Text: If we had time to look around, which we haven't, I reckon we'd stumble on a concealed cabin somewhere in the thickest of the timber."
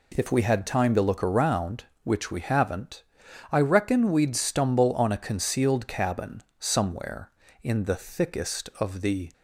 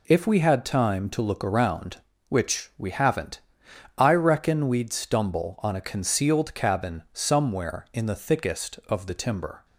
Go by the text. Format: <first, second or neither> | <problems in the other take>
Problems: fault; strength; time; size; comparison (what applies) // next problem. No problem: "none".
second | pauses between "cabin" and "somewhere"; slight; at 6.4 s; 0.16 s long // stops before "timber"; at 9.3 s